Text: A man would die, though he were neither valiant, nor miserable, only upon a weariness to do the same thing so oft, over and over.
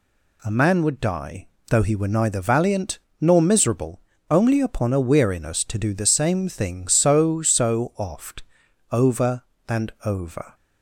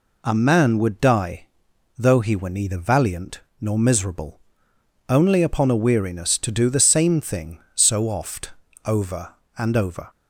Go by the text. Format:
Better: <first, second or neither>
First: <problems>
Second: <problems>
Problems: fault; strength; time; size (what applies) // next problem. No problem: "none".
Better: second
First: says "so" twice; at 7.4 s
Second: none